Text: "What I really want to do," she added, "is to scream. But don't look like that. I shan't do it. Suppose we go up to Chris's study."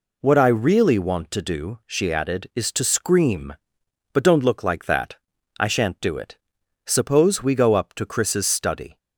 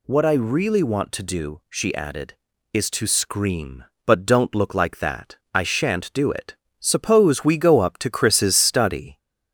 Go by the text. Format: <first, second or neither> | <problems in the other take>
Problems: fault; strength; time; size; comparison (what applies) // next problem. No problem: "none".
first | gets louder; slight; throughout; 2.5 dB